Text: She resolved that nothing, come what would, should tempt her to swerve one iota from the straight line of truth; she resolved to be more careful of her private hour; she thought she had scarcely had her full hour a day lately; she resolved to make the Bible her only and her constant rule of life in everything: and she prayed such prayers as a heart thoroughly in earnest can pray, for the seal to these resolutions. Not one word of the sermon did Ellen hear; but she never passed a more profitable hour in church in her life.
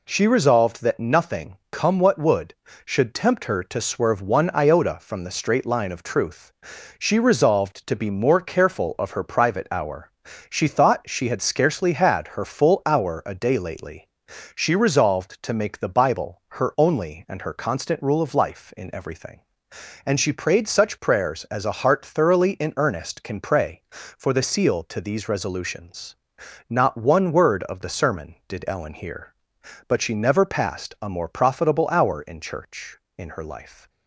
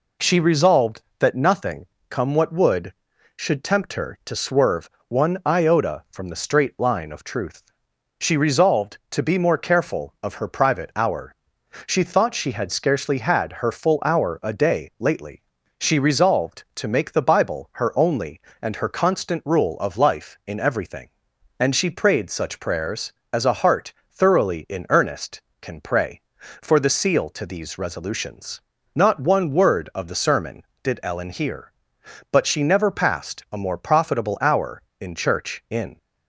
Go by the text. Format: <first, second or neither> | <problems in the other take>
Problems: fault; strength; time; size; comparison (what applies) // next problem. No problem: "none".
first | pauses between "swerve" and "one"; slight; at 4.8 s; 0.20 s long // pauses between "heart" and "thoroughly"; slight; at 23.9 s; 0.16 s long // stops before "her life"; at 35.9 s